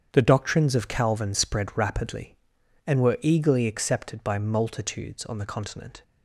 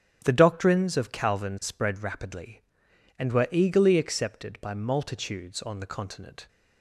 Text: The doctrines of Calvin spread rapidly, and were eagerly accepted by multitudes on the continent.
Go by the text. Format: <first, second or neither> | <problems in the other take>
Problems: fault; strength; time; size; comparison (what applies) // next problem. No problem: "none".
neither | starts louder than the rest; strong; the same in both